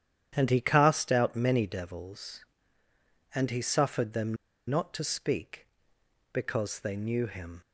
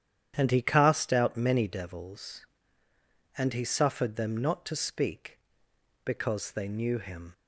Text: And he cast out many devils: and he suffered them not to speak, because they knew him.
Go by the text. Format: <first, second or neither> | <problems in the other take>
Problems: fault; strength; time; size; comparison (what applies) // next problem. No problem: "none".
second | starts louder than the rest; strong; until 1.3 s; 9.5 dB; strong in the second // pauses between "them" and "not"; slight; at 4.3 s; 0.33 s long